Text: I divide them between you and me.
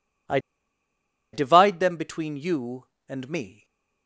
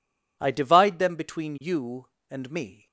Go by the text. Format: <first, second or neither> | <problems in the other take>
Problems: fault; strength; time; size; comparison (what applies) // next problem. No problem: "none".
second | pauses between "I" and "divide"; noticeable; at 0.3 s; 0.94 s long // stays silent after the last word; slight; from 3.5 s on; 0.5 s long